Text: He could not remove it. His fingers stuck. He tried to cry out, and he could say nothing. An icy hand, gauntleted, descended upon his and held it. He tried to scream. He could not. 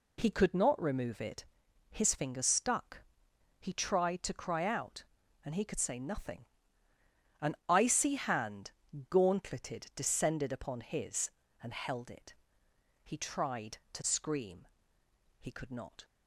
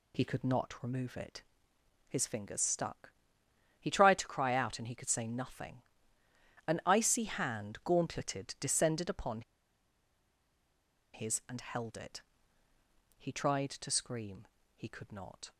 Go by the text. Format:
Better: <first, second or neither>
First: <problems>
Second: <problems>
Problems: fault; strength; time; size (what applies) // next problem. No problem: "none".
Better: first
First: none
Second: pauses between "upon" and "his"; strong; at 9.4 s; 1.7 s long